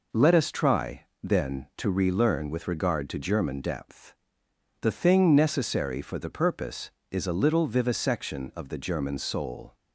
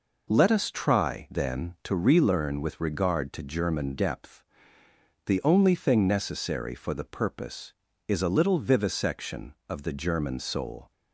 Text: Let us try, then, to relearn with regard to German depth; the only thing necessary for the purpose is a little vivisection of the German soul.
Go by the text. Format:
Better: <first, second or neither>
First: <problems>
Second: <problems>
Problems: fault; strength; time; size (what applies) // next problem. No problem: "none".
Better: second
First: skips "only"; at 4.9 s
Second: none